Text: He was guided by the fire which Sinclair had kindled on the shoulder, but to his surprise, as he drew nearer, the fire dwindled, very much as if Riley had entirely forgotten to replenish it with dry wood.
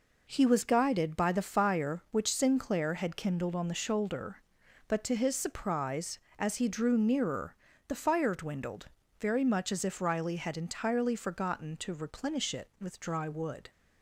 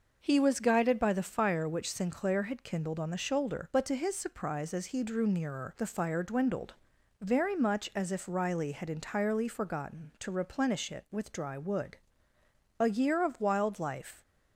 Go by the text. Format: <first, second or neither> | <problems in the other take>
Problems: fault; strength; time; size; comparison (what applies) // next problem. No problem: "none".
first | goes on to say "A year of wild life"; from 12.7 s on; 1.4 s long